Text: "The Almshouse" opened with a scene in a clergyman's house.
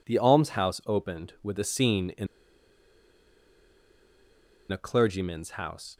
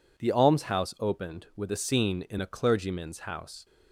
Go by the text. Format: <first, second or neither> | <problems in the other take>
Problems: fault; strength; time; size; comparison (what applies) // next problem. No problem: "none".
second | pauses between "in" and "a"; strong; at 2.2 s; 2.4 s long